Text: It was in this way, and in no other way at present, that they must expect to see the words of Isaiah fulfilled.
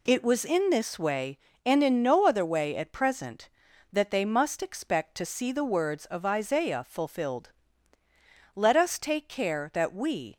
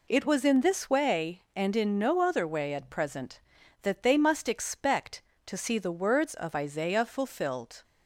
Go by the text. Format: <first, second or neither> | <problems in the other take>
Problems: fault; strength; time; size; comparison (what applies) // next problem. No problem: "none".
second | goes on to say "Let us take care that we"; strong; from 8.5 s on; 1.8 s long